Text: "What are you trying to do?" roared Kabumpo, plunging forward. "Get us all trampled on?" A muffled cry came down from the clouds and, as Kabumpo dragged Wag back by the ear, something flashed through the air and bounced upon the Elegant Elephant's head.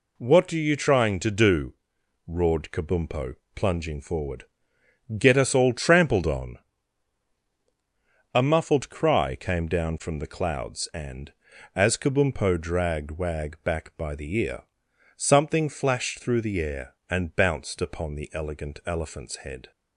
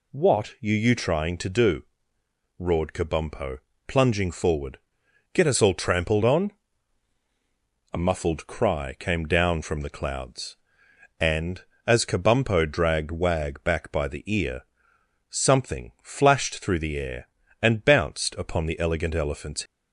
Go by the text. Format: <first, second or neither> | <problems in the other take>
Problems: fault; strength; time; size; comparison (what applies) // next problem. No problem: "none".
first | stops before "head"; at 19.6 s